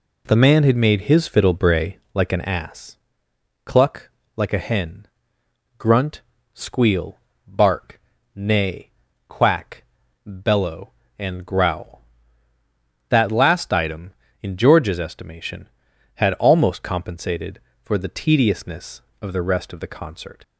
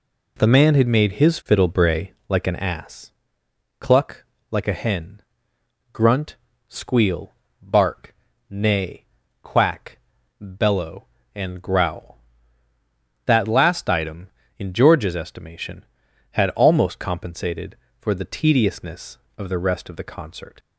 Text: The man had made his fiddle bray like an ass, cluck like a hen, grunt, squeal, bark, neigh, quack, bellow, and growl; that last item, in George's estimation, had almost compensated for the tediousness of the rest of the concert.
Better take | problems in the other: neither | pauses between "cluck" and "like"; slight; the same in both

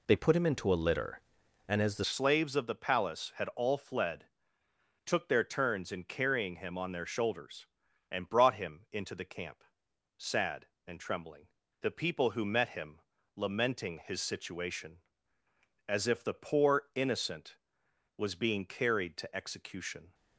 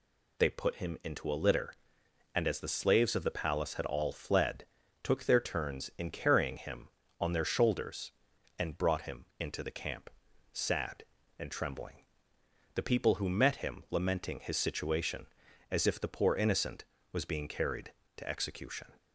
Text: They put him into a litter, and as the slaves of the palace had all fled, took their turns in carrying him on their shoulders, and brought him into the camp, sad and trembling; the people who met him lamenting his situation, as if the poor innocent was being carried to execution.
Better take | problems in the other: second | changes voice at "slaves"; from 2.0 s on; 18.1 s long // pauses between "him" and "lamenting"; slight; at 12.9 s; 0.36 s long

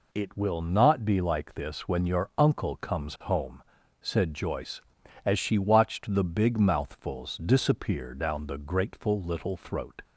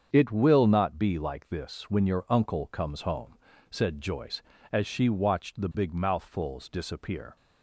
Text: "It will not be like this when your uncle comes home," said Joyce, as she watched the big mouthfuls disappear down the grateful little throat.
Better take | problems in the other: first | starts louder than the rest; strong; until 1.1 s; 7.5 dB // stops before "down the grateful little throat"; at 7.3 s

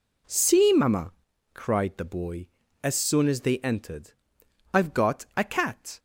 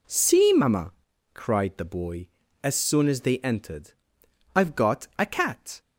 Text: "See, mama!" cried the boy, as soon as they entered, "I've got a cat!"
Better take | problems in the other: neither | none

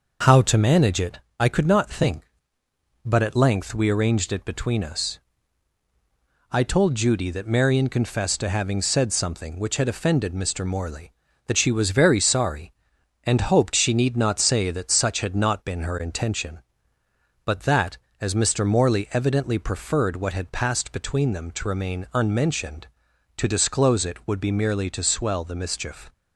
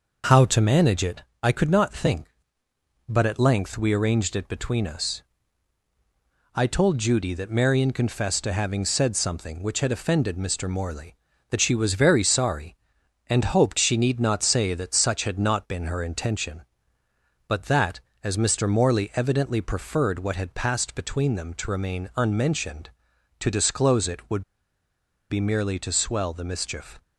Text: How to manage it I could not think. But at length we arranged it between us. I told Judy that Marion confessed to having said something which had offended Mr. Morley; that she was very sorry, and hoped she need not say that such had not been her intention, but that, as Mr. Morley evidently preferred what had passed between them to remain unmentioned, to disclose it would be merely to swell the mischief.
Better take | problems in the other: first | pauses between "it" and "I"; slight; at 1.2 s; 0.22 s long; slight in the first // pauses between "would" and "be"; noticeable; at 24.4 s; 0.89 s long

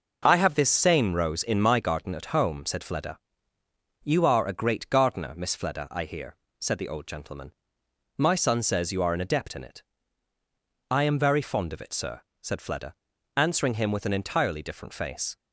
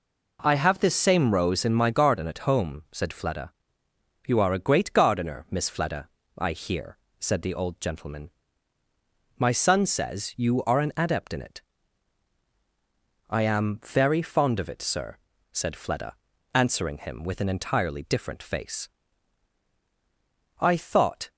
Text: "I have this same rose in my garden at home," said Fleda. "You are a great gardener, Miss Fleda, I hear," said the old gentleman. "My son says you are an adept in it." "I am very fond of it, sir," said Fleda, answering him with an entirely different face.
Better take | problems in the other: first | goes on to say "I thought"; noticeable; from 20.5 s on; 0.72 s long

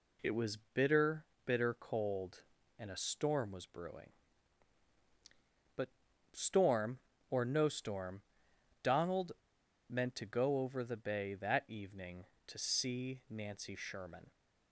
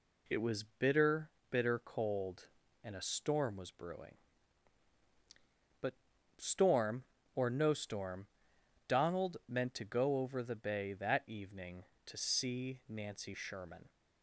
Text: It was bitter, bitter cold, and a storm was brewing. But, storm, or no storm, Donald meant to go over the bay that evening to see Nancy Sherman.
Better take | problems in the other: second | pauses between "was" and "bitter"; slight; at 0.5 s; 0.16 s long // pauses between "Donald" and "meant"; noticeable; at 9.3 s; 0.56 s long

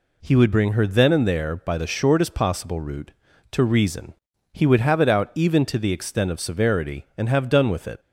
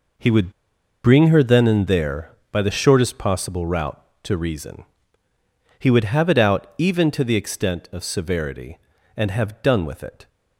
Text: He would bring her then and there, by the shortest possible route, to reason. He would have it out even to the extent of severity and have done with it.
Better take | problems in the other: first | pauses between "would" and "bring"; noticeable; at 0.5 s; 0.53 s long

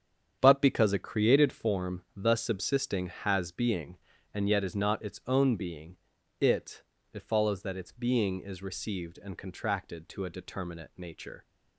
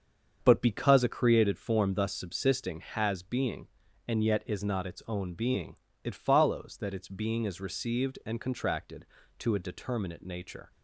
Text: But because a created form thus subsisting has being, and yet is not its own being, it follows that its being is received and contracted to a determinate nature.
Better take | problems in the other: second | starts louder than the rest; strong; until 1.4 s; 8 dB; also in the second // says "it" twice; at 7.1 s

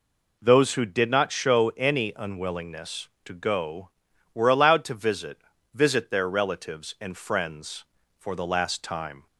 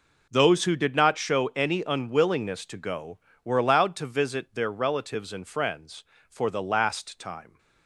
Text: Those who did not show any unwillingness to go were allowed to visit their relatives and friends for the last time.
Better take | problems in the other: second | says "visit" twice; at 5.7 s

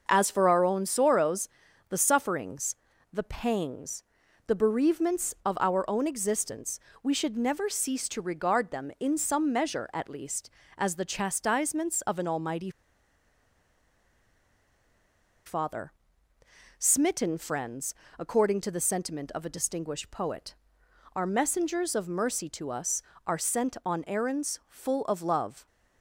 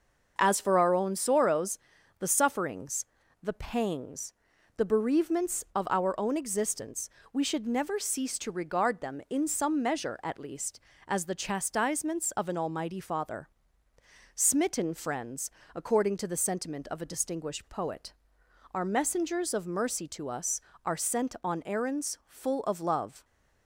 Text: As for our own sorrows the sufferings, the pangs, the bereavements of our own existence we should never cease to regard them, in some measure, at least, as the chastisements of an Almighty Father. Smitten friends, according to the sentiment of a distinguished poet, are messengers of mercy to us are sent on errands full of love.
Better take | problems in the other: second | starts louder than the rest; until 1.0 s; 6 dB; noticeable in the second // pauses between "sorrows" and "the"; at 1.4 s; 0.40 s long; also in the second // pauses between "existence" and "we"; slight; at 6.7 s; 0.24 s long; slight in the second // pauses between "Almighty" and "Father"; strong; at 12.7 s; 2.7 s long

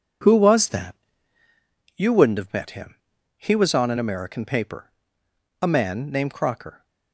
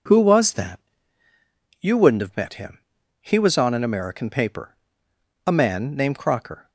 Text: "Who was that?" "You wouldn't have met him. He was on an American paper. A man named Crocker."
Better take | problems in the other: second | gets quieter; strong; throughout; 10.5 dB

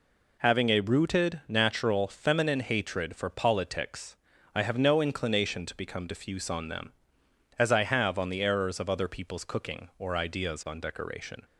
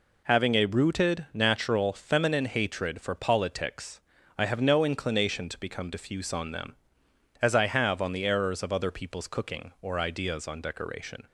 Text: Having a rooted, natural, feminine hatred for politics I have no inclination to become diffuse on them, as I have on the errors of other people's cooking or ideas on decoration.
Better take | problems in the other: neither | pauses between "politics" and "I"; the same in both

